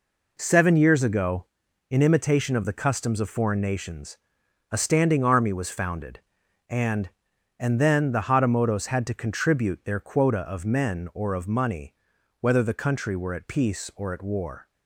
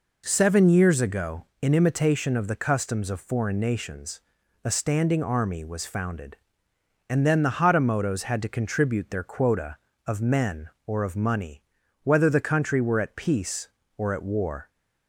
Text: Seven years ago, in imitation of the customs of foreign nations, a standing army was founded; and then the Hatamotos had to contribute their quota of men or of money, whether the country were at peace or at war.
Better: second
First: says "and" twice; at 7.5 s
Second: none

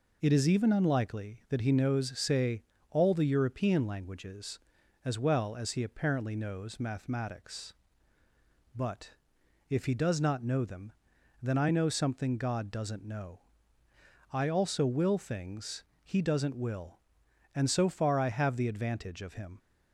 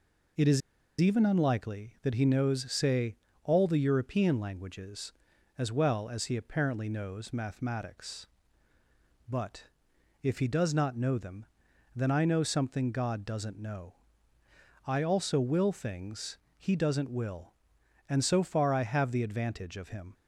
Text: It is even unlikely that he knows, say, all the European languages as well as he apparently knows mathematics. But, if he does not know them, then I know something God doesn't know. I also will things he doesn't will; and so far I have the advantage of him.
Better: first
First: pauses between "things" and "he"; slight; at 15.8 s; 0.20 s long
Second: pauses between "is" and "even"; at 0.6 s; 0.40 s long // pauses between "things" and "he"; slight; at 16.3 s; 0.20 s long

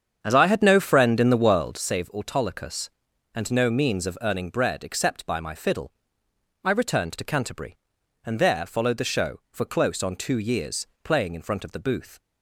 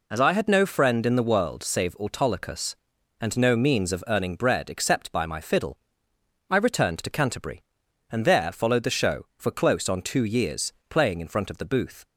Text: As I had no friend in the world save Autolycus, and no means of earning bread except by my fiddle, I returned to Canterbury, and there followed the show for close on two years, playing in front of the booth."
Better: second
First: starts louder than the rest; strong; until 1.8 s; 8 dB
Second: none

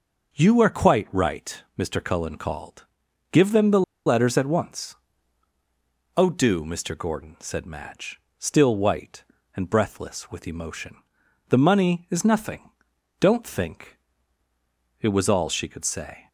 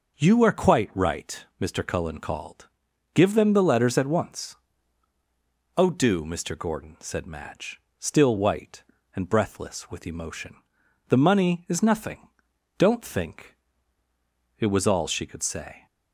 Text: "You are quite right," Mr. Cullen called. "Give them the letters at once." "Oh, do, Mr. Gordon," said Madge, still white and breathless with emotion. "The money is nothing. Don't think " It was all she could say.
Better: second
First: pauses between "the" and "letters"; slight; at 3.8 s; 0.25 s long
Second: none

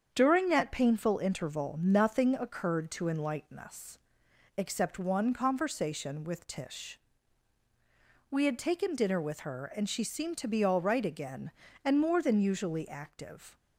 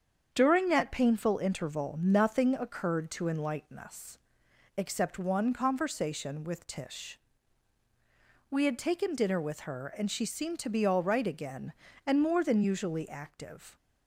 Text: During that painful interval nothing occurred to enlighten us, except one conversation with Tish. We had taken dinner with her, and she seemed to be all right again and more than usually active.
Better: neither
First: starts louder than the rest; strong; until 1.1 s; 7.5 dB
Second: starts louder than the rest; strong; until 1.3 s; 7.5 dB

